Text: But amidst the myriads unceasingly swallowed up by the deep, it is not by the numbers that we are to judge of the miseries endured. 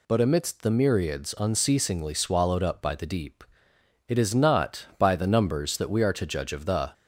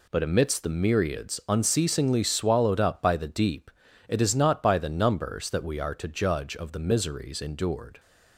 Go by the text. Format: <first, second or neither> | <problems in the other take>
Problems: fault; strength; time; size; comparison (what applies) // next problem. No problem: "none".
second | stops before "miseries endured"; at 6.9 s